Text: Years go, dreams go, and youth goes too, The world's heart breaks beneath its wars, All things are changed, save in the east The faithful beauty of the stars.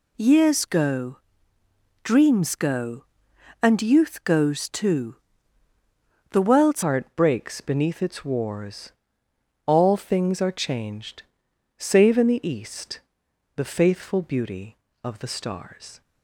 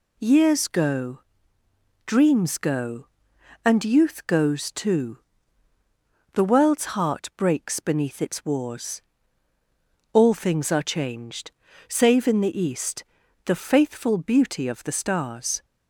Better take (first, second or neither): second